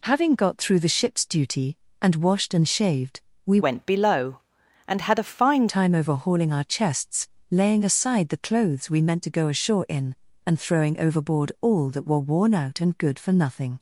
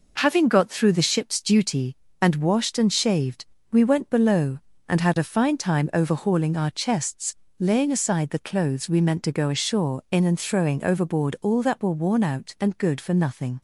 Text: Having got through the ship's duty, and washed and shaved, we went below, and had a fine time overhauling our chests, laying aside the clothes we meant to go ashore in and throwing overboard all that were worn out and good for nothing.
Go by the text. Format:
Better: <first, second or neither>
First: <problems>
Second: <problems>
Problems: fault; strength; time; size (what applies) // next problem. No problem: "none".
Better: second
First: changes voice from "went" to "fine"; from 3.6 to 5.6 s; 2.0 s long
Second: none